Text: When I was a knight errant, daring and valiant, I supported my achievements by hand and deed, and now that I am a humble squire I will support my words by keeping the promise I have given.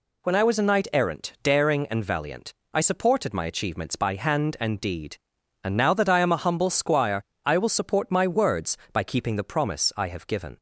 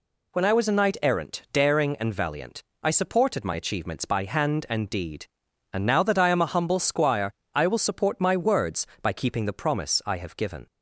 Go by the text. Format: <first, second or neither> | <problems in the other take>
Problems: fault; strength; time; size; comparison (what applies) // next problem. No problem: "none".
neither | pauses between "squire" and "I"; slight; the same in both